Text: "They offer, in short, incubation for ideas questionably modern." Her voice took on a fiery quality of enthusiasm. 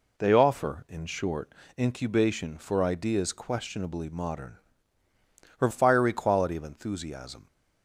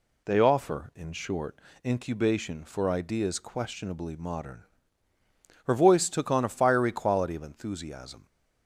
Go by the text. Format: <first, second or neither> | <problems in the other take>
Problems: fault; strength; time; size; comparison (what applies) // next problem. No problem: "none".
second | skips "voice took on a"; at 5.6 s